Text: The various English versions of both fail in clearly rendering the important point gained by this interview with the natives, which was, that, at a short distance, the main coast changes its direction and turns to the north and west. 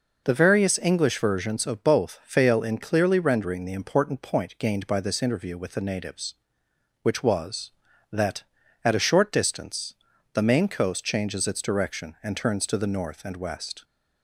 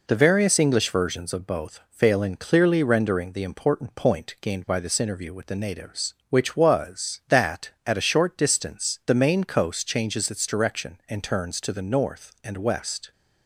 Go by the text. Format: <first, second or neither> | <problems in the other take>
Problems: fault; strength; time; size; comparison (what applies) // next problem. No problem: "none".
neither | none